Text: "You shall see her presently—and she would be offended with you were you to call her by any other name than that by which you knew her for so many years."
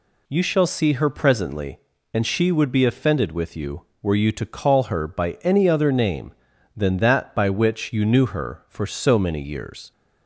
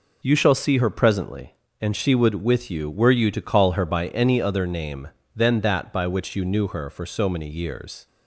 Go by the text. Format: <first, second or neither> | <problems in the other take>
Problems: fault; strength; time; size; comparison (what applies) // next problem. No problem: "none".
first | skips "be offended"; at 2.3 s